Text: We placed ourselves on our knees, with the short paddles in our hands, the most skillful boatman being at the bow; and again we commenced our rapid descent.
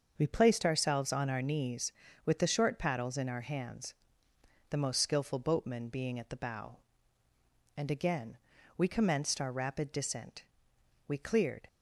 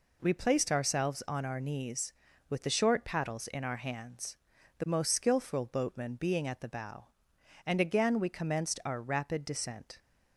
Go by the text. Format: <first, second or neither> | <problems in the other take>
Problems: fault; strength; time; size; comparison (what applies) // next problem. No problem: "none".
second | starts louder than the rest; until 1.1 s; 6.5 dB // pauses between "again" and "we"; at 8.3 s; 0.40 s long // goes on to say "We cleared"; from 11.0 s on; 0.58 s long